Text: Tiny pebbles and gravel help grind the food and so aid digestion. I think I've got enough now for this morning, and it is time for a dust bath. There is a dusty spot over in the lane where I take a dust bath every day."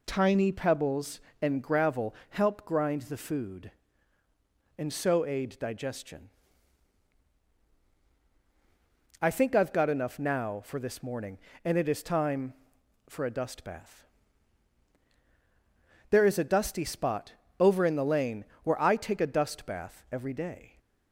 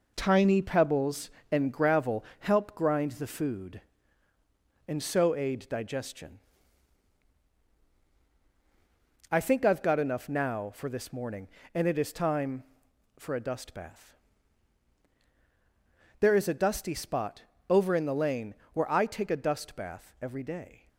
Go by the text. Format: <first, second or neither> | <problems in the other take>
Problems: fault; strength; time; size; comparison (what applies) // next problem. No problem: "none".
first | gets quieter; throughout; 6.5 dB // pauses between "gravel" and "help"; slight; at 2.2 s; 0.16 s long; slight in the first // pauses between "spot" and "over"; slight; at 17.4 s; 0.26 s long; slight in the first // pauses between "lane" and "where"; slight; at 18.5 s; 0.20 s long; slight in the first